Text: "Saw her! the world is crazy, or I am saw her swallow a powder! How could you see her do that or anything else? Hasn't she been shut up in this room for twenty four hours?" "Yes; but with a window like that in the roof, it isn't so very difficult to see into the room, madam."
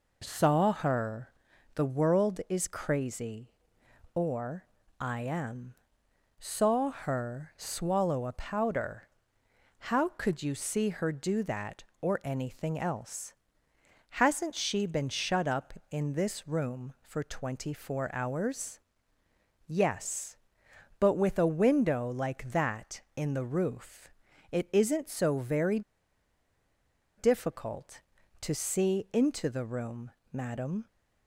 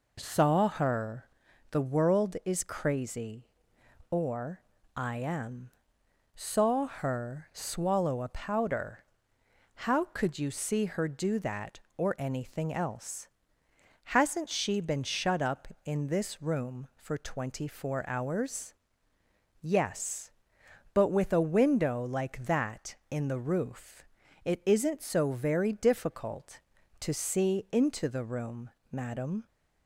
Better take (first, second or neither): second